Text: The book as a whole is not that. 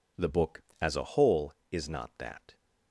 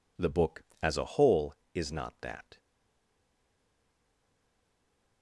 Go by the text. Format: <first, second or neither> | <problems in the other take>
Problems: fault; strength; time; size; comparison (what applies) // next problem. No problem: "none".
first | stays silent after the last word; strong; from 2.5 s on; 2.7 s long